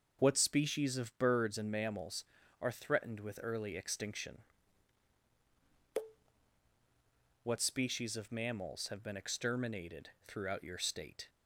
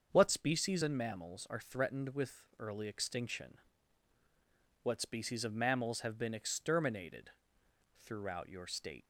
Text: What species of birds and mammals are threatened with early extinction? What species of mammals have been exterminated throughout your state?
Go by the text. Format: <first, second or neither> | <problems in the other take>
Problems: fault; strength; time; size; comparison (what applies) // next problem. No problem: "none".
first | starts louder than the rest; until 1.1 s; 6.5 dB // skips "of birds"; at 0.8 s // pauses between "with" and "early"; slight; at 2.4 s; 0.16 s long // pauses between "exterminated" and "throughout"; noticeable; at 7.3 s; 0.74 s long; slight in the first